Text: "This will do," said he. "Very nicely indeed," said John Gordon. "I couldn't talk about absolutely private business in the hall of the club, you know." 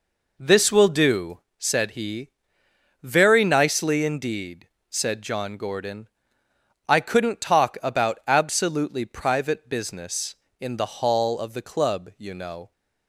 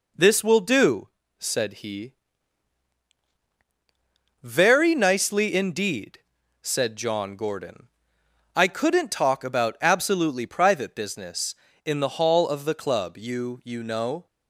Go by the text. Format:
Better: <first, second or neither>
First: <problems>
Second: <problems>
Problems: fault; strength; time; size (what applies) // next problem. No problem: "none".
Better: first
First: none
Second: says "you" twice; at 13.6 s